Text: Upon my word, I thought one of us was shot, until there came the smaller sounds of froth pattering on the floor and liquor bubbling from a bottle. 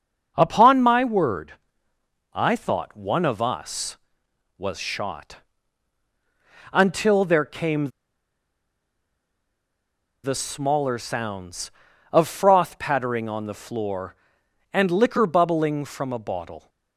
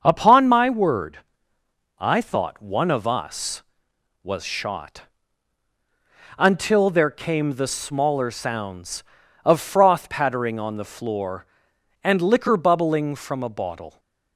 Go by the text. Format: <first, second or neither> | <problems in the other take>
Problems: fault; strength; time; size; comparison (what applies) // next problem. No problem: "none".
second | starts louder than the rest; until 1.3 s; 6.5 dB; also in the second // pauses between "came" and "the"; strong; at 7.8 s; 2.3 s long